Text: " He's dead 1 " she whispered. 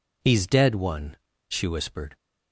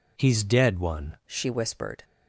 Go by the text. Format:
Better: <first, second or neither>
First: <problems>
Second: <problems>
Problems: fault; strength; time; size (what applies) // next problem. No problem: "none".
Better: first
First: none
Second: changes voice at "she"; from 1.2 s on; 0.8 s long